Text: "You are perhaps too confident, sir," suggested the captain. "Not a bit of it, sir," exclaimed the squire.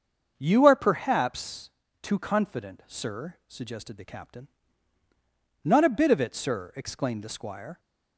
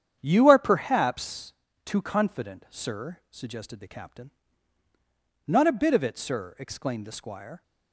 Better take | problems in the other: first | gets quieter; strong; throughout; 8.5 dB // starts louder than the rest; strong; until 1.2 s; 9 dB; also in the first // pauses between "perhaps" and "too"; slight; at 1.5 s; 0.32 s long; slight in the first

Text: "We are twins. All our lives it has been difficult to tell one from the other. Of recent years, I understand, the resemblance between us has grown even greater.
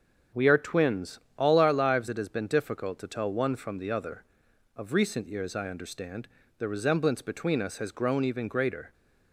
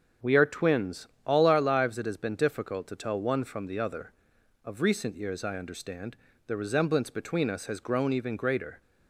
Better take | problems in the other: neither | starts louder than the rest; strong; the same in both

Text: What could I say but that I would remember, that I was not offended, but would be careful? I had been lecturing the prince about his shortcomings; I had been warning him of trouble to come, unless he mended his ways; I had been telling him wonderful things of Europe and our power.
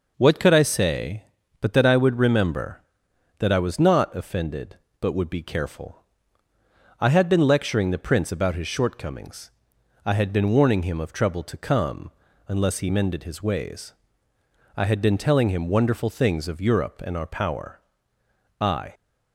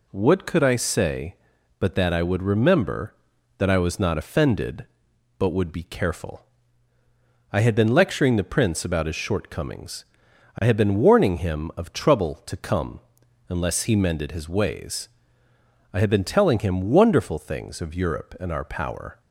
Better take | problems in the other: second | goes on to say "I"; slight; from 18.6 s on; 0.32 s long

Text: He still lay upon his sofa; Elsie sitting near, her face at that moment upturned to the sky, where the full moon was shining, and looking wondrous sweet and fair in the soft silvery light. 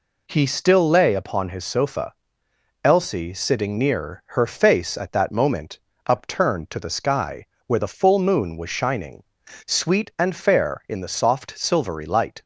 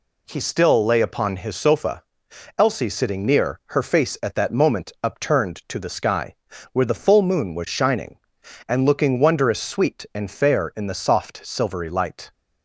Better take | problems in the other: second | pauses between "moment" and "upturned"; slight; at 5.7 s; 0.26 s long // skips "and looking wondrous"; at 9.4 s

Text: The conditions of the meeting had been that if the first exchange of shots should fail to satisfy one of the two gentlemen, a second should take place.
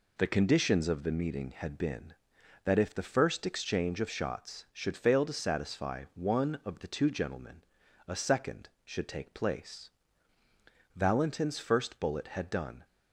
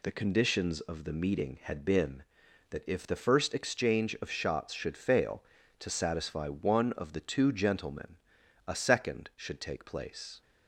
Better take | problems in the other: second | goes on to say "Valentin's first bullet had done"; strong; from 10.9 s on; 1.9 s long

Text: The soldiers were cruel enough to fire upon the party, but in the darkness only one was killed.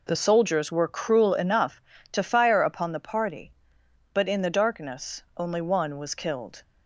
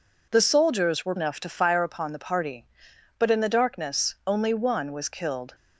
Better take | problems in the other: first | skips "cruel"; at 1.1 s

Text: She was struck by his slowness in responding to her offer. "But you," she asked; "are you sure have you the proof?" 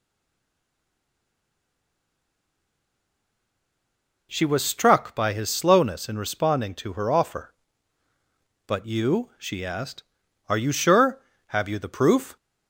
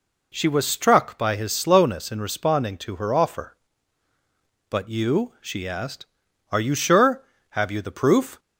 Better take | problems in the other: second | stays silent before the first word; strong; until 4.2 s; 4.2 s long

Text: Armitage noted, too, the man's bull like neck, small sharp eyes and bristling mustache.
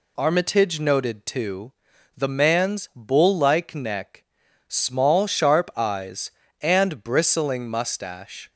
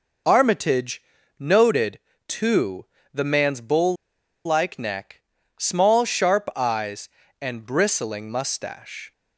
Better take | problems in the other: first | pauses between "Armitage" and "noted"; slight; at 1.0 s; 0.36 s long // pauses between "bull" and "like"; noticeable; at 3.9 s; 0.51 s long

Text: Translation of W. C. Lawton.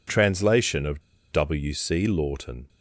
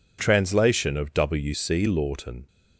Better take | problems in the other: second | pauses between "of" and "W"; slight; at 1.0 s; 0.30 s long

